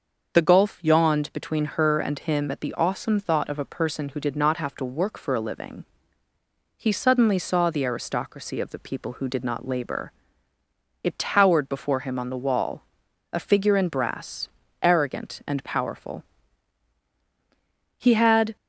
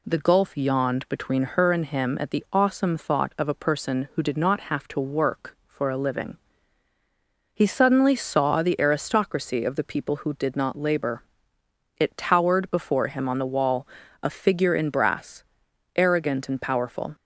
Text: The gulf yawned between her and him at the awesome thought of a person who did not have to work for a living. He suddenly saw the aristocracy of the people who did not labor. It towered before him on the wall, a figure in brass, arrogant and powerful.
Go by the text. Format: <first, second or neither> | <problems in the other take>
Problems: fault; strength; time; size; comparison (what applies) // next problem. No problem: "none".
second | starts louder than the rest; until 1.4 s; 6.5 dB // goes on to say "He had"; from 17.9 s on; 0.58 s long